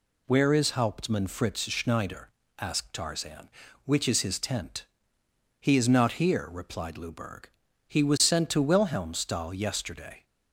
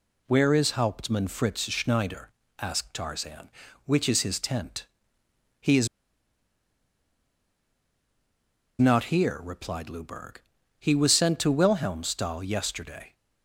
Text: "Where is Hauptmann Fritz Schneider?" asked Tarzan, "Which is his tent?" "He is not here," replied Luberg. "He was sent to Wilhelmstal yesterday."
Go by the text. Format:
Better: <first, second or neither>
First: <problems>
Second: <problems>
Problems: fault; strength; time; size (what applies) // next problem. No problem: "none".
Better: first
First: none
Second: pauses between "is" and "not"; strong; at 5.8 s; 2.9 s long